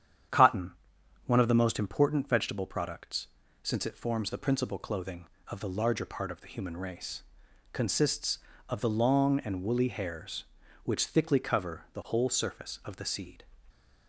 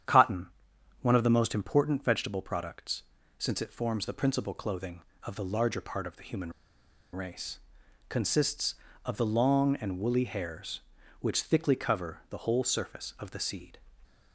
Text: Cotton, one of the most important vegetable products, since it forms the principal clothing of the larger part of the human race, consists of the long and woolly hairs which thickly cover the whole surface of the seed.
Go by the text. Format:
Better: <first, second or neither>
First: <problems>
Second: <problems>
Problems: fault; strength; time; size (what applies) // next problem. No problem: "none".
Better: first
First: starts louder than the rest; strong; until 1.8 s; 9 dB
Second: starts louder than the rest; strong; until 1.5 s; 9 dB // pauses between "human" and "race"; noticeable; at 6.5 s; 0.61 s long